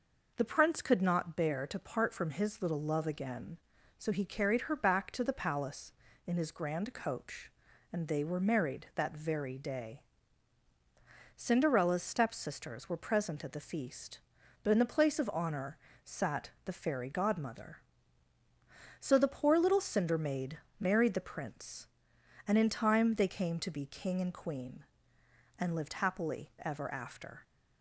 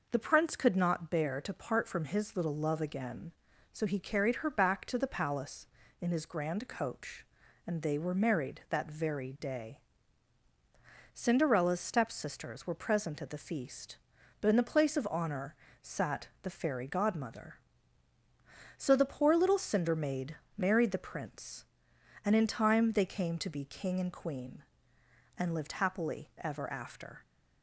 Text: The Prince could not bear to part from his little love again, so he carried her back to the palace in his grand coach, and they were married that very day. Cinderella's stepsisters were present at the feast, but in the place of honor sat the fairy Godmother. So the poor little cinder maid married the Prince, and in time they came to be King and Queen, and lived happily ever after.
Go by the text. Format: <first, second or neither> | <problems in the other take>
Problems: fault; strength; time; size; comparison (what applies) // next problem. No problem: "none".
neither | pauses between "honor" and "sat"; slight; the same in both // pauses between "sat" and "the"; slight; the same in both // pauses between "maid" and "married"; slight; the same in both